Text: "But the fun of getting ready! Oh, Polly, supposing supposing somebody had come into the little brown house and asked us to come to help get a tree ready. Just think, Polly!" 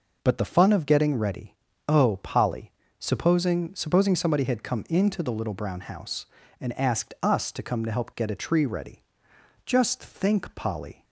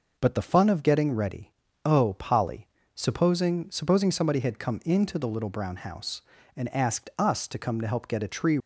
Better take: first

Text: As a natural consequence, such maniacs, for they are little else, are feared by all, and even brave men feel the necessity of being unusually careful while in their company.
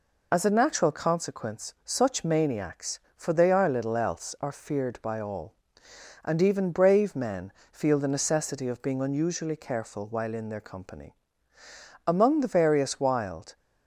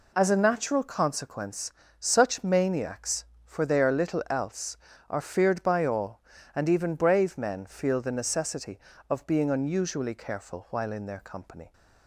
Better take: second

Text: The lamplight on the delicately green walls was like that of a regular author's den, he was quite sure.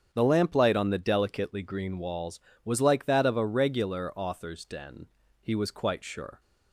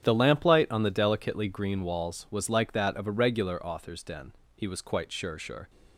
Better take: first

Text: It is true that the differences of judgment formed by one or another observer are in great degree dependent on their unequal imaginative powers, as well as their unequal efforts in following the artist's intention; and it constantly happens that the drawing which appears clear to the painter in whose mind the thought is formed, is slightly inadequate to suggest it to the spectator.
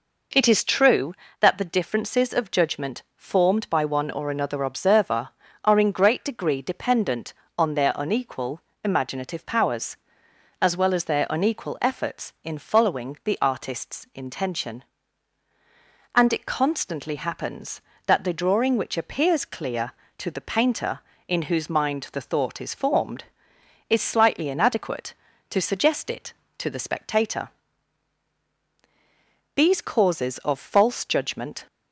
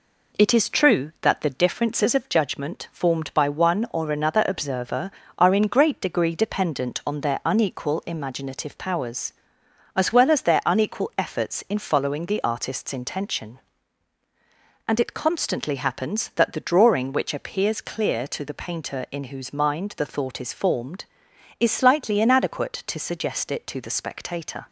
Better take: second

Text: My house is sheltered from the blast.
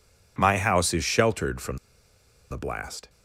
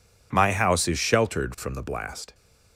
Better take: second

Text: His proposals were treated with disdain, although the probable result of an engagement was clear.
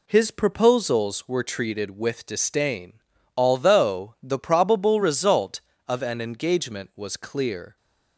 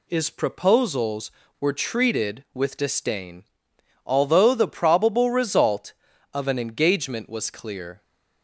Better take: first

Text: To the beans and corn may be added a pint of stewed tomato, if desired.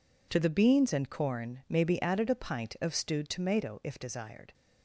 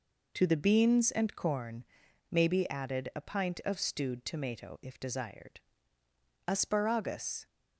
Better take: first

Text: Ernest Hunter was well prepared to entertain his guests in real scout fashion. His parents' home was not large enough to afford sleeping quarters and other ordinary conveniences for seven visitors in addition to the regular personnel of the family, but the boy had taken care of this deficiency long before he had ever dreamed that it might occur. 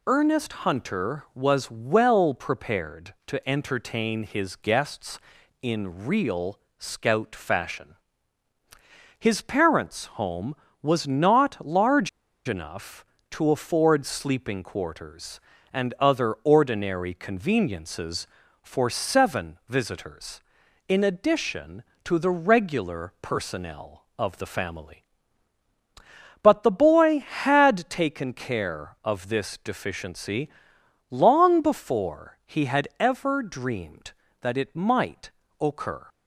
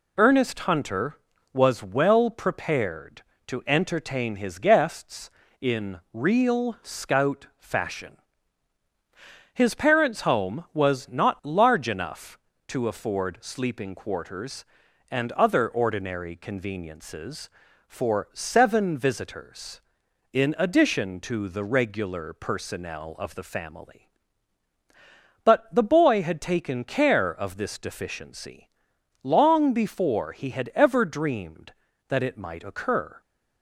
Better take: second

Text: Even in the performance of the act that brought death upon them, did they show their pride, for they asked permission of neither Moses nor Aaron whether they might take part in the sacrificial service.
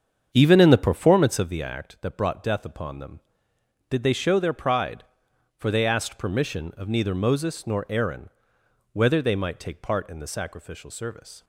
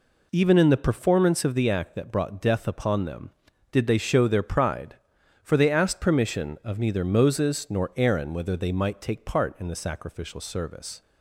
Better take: second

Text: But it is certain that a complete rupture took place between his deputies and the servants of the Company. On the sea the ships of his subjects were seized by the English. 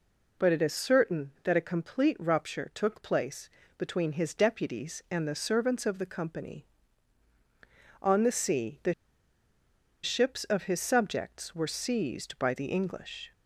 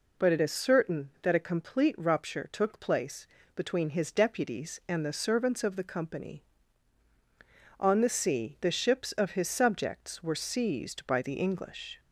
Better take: second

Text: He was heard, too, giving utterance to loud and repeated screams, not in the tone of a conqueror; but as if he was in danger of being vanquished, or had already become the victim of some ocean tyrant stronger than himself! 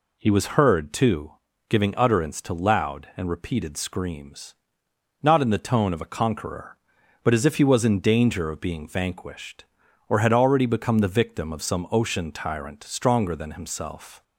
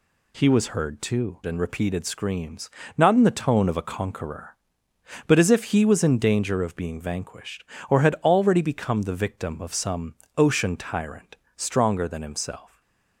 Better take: first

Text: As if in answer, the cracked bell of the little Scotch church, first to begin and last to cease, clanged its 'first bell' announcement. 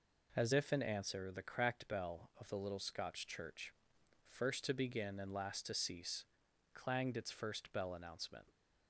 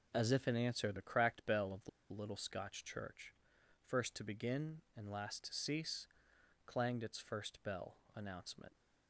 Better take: first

